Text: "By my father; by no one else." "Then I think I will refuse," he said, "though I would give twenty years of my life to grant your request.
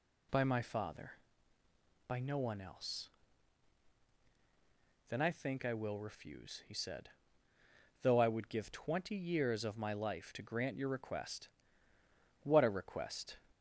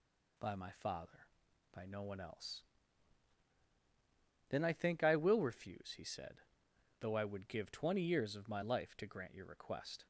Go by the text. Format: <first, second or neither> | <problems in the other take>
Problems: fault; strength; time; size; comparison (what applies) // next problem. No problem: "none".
second | goes on to say "What a request"; noticeable; from 12.4 s on; 0.94 s long